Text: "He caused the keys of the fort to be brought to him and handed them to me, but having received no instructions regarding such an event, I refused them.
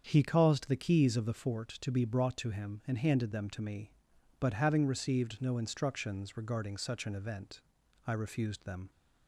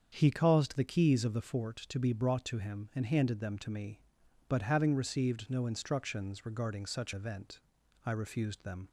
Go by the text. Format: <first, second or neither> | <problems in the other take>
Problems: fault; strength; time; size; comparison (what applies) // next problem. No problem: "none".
first | starts louder than the rest; strong; until 1.1 s; 7.5 dB; strong in the first // skips "an"; at 7.1 s